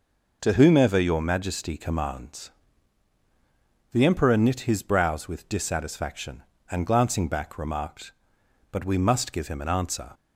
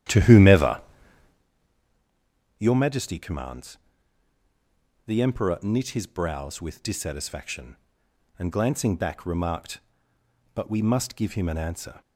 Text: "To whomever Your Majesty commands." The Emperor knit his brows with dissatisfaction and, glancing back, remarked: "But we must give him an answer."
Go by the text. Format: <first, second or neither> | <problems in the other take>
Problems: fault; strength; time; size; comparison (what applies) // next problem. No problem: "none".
first | starts louder than the rest; strong; until 1.5 s; 11.5 dB // pauses between "whomever" and "Your"; strong; at 0.8 s; 1.7 s long